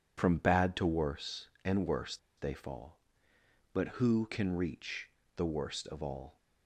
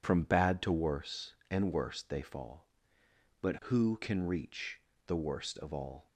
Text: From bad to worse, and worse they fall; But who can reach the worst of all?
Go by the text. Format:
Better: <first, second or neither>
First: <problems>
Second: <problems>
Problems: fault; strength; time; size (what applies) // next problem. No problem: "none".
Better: second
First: pauses between "worse" and "they"; slight; at 2.1 s; 0.20 s long // pauses between "reach" and "the"; slight; at 5.0 s; 0.28 s long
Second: pauses between "reach" and "the"; slight; at 4.7 s; 0.28 s long